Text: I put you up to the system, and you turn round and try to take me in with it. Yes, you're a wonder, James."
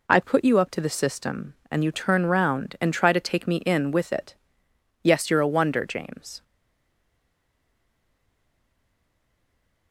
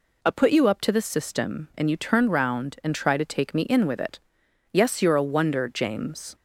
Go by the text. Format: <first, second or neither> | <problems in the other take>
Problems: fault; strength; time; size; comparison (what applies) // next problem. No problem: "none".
second | stays silent after the last word; strong; from 6.4 s on; 3.5 s long